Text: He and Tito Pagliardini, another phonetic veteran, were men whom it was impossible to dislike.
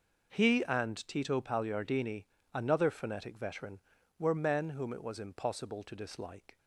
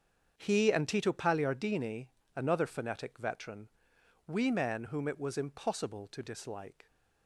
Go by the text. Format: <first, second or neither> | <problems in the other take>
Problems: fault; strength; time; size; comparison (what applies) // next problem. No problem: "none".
first | starts louder than the rest; until 1.3 s; 7 dB // says "we" for "were"; at 4.2 s